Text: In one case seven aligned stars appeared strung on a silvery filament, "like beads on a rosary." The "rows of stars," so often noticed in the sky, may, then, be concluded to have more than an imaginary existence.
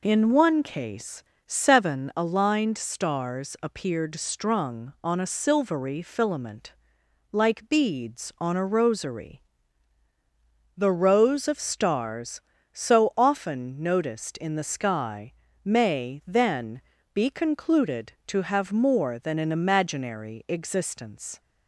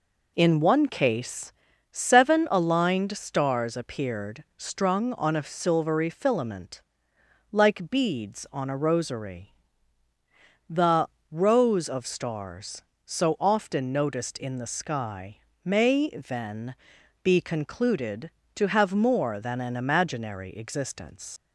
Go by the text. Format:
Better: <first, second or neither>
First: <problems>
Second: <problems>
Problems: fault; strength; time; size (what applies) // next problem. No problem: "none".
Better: first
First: pauses between "case" and "seven"; slight; at 1.2 s; 0.22 s long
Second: pauses between "case" and "seven"; at 1.5 s; 0.40 s long // pauses between "The" and "rows"; slight; at 11.0 s; 0.22 s long // leaves "existence" unfinished; at 21.3 s; 90 ms